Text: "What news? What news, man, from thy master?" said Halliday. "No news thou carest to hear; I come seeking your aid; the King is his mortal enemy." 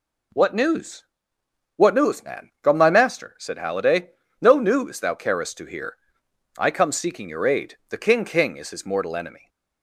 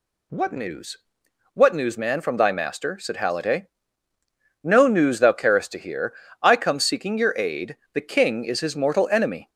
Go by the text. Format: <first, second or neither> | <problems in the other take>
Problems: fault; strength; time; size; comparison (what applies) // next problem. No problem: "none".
second | says "King" twice; at 8.2 s